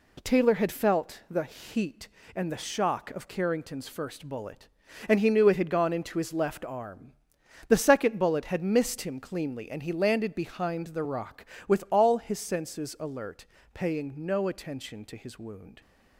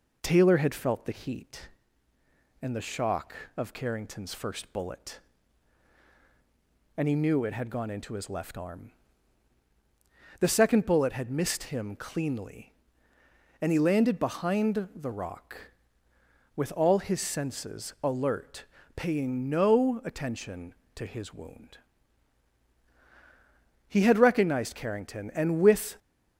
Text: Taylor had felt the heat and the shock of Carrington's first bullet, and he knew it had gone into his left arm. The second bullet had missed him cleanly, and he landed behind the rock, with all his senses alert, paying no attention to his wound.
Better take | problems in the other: first | goes on to say "He had recognized Carrington and with"; strong; from 23.8 s on; 2.1 s long

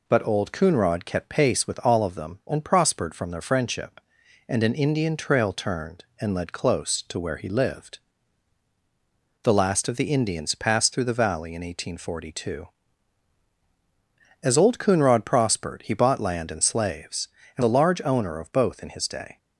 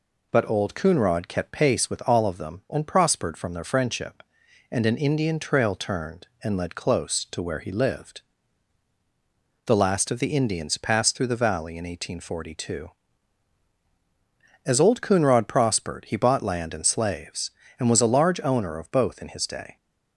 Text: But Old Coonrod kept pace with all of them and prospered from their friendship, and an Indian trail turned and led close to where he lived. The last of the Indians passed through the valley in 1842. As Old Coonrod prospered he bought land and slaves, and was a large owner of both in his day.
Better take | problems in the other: second | skips "was"; at 17.6 s

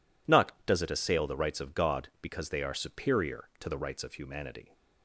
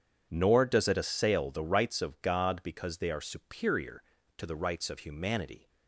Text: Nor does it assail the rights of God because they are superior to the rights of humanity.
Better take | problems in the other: second | says "Not" for "Nor"; at 0.2 s

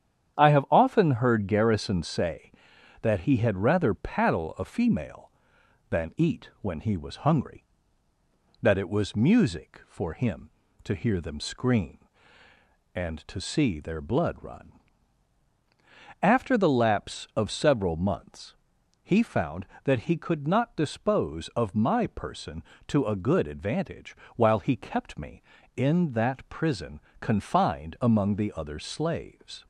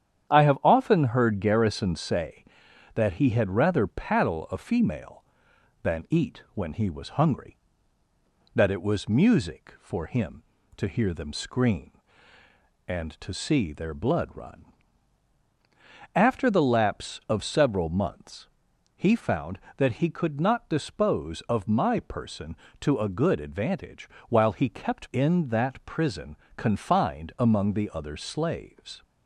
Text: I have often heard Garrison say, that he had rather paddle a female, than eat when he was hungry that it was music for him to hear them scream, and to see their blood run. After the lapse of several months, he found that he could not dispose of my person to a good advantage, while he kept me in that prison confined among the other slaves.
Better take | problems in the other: first | starts louder than the rest; strong; until 1.3 s; 9.5 dB; strong in the first // skips "me"; at 25.1 s // pauses between "prison" and "confined"; slight; at 26.3 s; 0.20 s long; slight in the first

